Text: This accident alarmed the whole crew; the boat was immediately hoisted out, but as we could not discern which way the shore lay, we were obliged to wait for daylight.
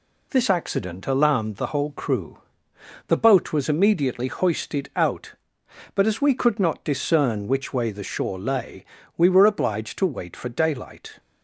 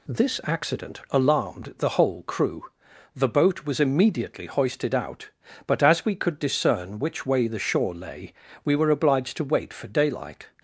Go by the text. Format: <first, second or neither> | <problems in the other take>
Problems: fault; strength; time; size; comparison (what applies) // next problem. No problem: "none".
first | skips "not"; at 6.3 s